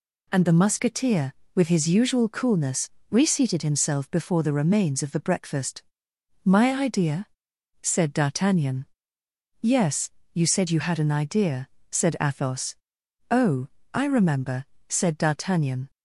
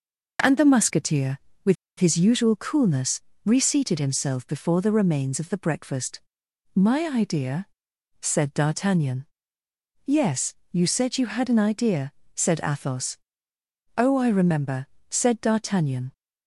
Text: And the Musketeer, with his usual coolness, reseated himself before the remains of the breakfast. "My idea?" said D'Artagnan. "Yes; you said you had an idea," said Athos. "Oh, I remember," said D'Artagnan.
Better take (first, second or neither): first